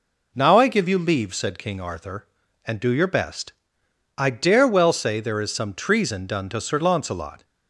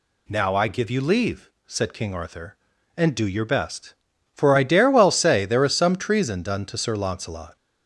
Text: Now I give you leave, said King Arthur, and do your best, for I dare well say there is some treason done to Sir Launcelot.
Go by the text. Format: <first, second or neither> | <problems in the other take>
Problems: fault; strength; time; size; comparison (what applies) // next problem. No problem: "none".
second | skips "for"; at 3.8 s